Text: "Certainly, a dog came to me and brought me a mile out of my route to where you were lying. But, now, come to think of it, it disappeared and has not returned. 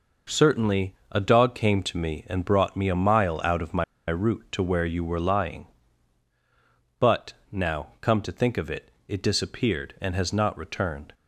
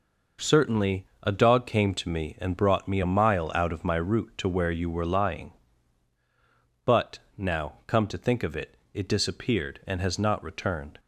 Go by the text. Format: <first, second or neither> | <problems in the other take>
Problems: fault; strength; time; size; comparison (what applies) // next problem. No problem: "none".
second | pauses between "my" and "route"; slight; at 3.8 s; 0.25 s long